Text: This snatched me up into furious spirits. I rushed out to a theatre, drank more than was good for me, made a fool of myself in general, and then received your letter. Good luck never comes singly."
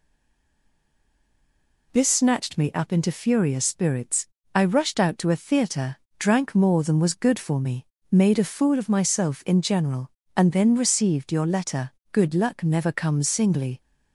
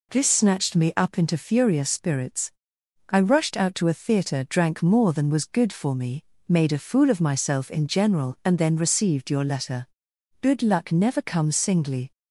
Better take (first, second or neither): second